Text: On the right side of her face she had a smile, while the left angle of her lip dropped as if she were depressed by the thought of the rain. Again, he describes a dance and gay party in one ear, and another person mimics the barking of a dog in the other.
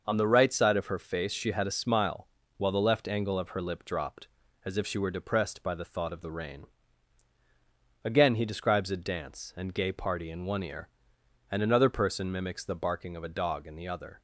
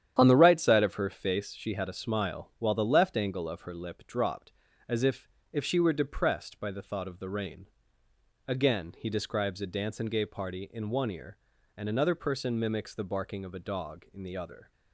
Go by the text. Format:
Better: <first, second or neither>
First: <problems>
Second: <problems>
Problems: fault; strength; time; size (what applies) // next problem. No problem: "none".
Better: first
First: none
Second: starts louder than the rest; strong; until 1.2 s; 10 dB // says "if" twice; at 5.5 s